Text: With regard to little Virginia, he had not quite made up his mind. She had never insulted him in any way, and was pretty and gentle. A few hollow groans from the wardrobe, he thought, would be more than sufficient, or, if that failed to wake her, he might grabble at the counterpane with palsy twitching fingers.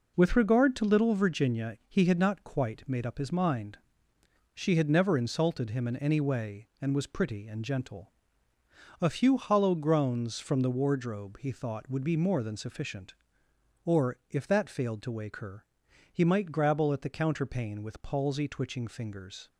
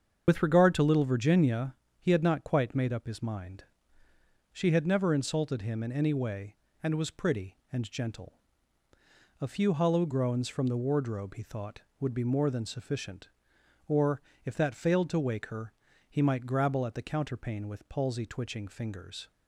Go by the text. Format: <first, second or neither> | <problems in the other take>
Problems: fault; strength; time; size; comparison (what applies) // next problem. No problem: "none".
first | loses the start of "With"; at 0.2 s; 60 ms // starts louder than the rest; strong; until 1.2 s; 7.5 dB